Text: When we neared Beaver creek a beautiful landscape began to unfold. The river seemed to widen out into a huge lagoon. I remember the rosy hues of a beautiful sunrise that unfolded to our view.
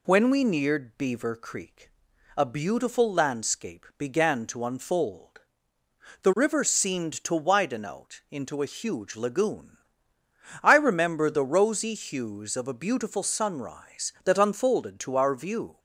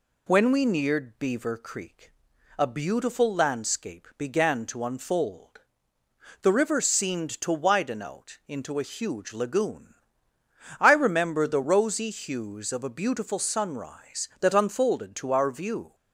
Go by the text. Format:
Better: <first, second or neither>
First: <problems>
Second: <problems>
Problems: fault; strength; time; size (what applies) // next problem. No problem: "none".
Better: neither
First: pauses between "creek" and "a"; noticeable; at 1.8 s; 0.48 s long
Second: pauses between "creek" and "a"; noticeable; at 2.1 s; 0.48 s long